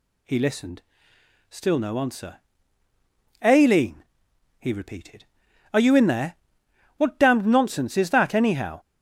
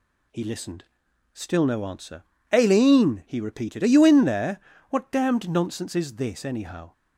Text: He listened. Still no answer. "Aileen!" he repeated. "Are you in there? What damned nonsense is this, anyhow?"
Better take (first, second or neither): second